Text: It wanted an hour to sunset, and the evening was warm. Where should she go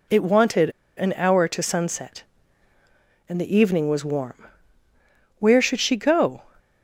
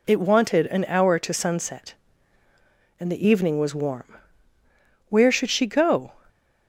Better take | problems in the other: second | pauses between "wanted" and "an"; slight; at 0.6 s; 0.27 s long

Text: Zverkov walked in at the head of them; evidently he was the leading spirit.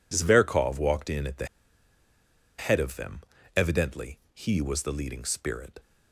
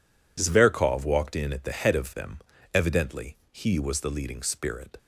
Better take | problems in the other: second | pauses between "the" and "head"; at 1.4 s; 1.1 s long

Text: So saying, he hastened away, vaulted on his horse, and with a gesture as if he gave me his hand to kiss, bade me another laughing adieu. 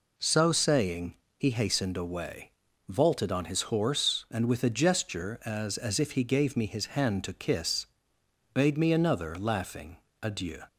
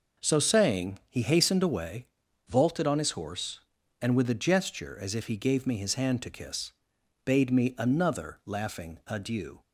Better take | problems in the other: second | says "as" twice; at 5.7 s // pauses between "laughing" and "adieu"; slight; at 9.9 s; 0.24 s long

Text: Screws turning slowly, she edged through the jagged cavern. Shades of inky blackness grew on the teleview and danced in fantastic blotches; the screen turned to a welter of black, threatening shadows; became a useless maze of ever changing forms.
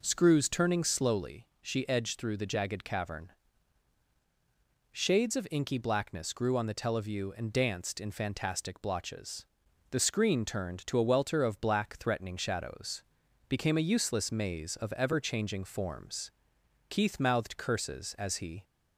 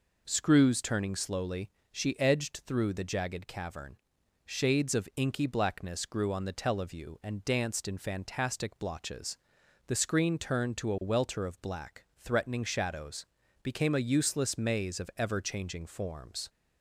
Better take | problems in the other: second | goes on to say "Keith mouthed curses as he"; strong; from 16.8 s on; 1.7 s long

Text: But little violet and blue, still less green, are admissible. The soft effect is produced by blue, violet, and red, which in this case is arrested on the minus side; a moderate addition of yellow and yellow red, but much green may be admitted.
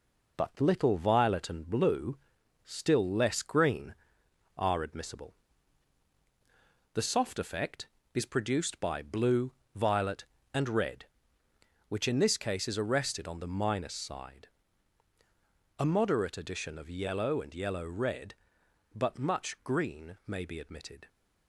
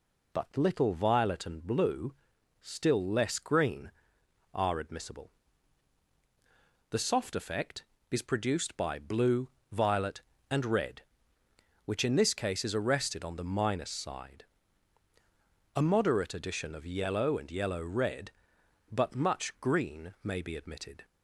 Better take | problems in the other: second | gets quieter; noticeable; throughout; 5.5 dB

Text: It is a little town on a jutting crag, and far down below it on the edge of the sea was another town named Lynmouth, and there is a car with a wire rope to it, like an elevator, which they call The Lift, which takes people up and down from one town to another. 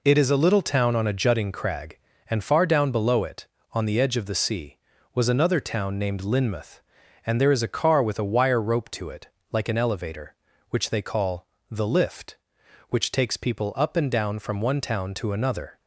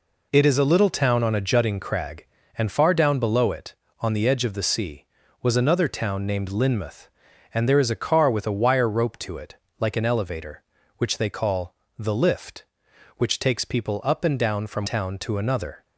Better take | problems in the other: first | pauses between "call" and "The"; slight; at 11.7 s; 0.24 s long; slight in the first // skips "one"; at 14.8 s

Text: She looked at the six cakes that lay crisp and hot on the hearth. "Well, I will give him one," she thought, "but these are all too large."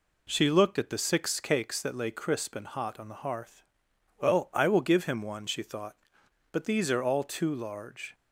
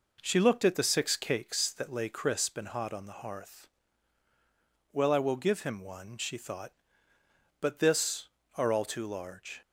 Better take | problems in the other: first | says "this" for "these"; at 7.7 s

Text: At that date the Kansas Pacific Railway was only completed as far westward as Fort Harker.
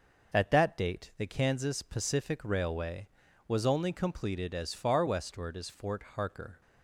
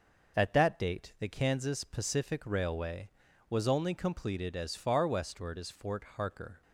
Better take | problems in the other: neither | none

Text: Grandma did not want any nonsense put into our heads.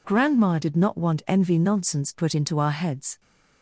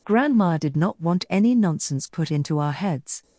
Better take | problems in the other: second | says "envy" for "any"; at 1.2 s

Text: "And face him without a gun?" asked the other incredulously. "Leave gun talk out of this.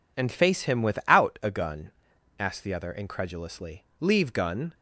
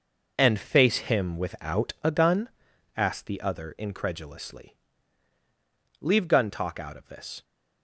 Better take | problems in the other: second | stops before "talk out of this"; at 4.7 s

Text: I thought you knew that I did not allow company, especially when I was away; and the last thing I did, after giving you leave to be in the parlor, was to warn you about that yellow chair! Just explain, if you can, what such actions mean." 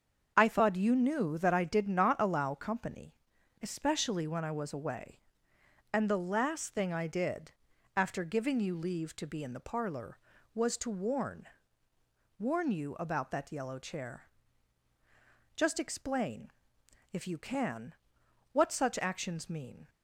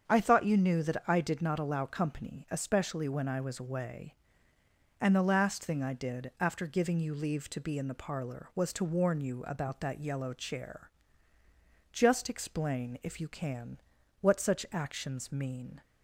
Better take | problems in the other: second | starts louder than the rest; until 1.3 s; 6.5 dB; strong in the second // says "warn" twice; at 12.3 s

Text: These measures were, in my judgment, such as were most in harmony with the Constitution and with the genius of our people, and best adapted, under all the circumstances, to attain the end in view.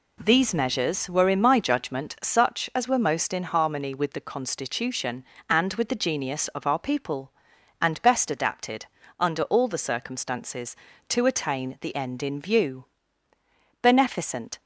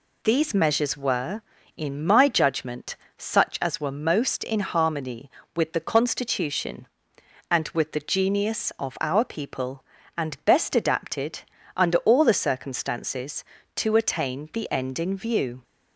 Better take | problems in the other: second | goes on to say "Beneficent"; noticeable; from 13.8 s on; 0.80 s long

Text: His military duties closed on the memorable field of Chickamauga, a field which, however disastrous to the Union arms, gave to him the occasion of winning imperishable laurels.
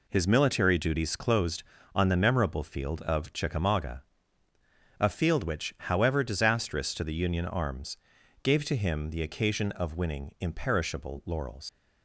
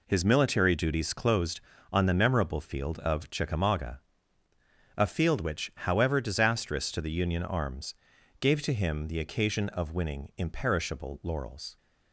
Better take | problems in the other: second | leaves "laurels" unfinished; at 11.6 s; 100 ms

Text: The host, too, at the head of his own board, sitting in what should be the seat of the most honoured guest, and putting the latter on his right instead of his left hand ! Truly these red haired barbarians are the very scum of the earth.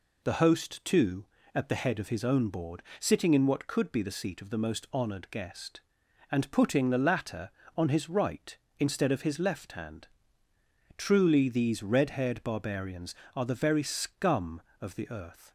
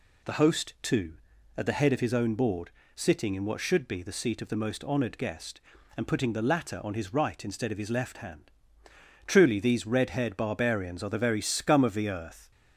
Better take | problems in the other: second | says "could" for "should"; at 3.6 s

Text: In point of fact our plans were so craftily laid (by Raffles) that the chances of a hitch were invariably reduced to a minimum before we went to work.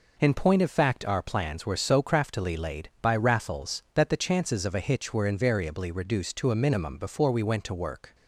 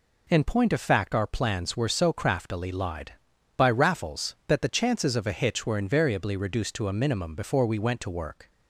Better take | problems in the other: first | says "lied" for "laid"; at 2.6 s

